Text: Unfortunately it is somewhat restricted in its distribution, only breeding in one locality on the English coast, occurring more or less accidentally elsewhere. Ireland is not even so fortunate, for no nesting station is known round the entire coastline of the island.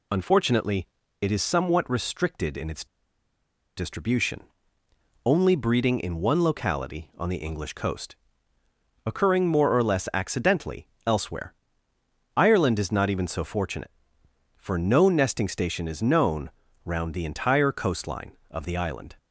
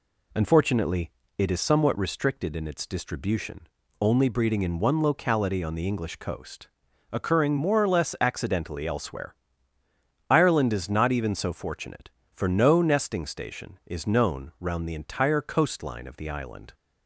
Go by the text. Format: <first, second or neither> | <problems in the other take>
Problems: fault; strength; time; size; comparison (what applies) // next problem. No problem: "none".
second | pauses between "Unfortunately" and "it"; slight; at 0.8 s; 0.34 s long; slight in the second // pauses between "its" and "distribution"; noticeable; at 2.8 s; 0.91 s long // pauses between "accidentally" and "elsewhere"; slight; at 10.8 s; 0.18 s long // pauses between "known" and "round"; slight; at 16.5 s; 0.34 s long